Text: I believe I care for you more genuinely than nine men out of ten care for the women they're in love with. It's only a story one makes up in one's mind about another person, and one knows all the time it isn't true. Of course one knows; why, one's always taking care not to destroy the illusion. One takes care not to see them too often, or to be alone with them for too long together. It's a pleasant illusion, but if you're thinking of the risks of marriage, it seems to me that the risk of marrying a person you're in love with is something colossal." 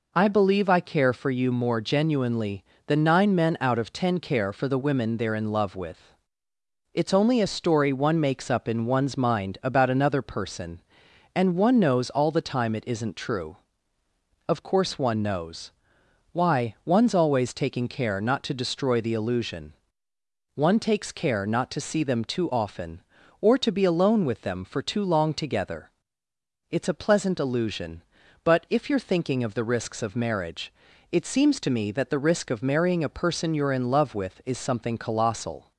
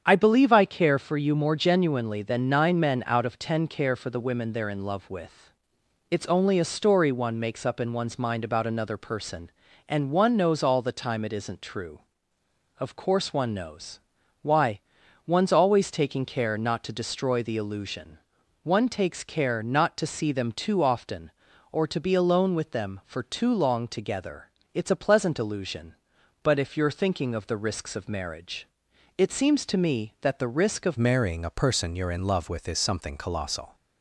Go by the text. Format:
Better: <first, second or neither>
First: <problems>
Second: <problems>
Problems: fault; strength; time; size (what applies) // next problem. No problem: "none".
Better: first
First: none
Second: starts louder than the rest; strong; until 1.0 s; 8 dB // changes voice at "marrying"; from 30.9 s on; 2.8 s long